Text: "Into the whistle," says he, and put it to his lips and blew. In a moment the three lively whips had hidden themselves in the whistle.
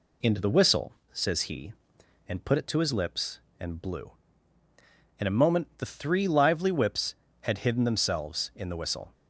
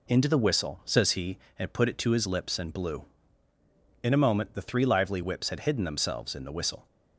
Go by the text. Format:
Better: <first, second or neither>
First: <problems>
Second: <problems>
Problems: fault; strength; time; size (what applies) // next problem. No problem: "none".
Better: neither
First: none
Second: none